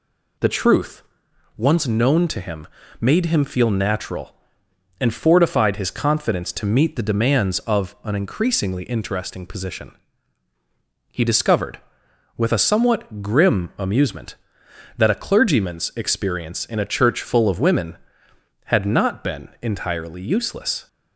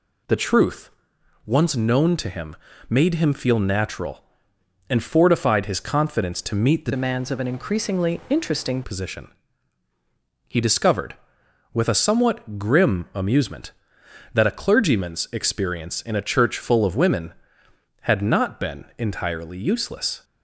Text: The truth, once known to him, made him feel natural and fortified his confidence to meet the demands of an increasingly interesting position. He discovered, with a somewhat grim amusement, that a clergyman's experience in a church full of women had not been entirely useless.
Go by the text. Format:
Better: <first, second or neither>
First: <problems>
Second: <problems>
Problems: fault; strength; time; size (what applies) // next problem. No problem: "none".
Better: first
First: none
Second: changes voice from "demands" to "interesting"; from 6.9 to 8.8 s; 1.9 s long